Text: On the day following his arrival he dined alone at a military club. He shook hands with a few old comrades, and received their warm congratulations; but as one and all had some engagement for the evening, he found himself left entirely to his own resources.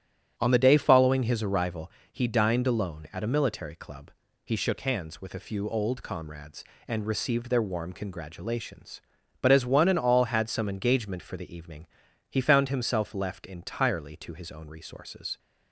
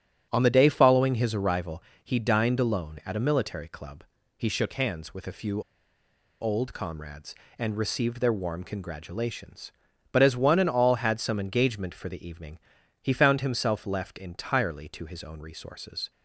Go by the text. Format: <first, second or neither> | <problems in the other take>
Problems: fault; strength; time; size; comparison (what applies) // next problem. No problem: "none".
first | starts louder than the rest; strong; until 1.3 s; 9 dB; strong in the first // pauses between "arrival" and "he"; slight; at 1.8 s; 0.22 s long; slight in the first // pauses between "few" and "old"; noticeable; at 5.6 s; 0.78 s long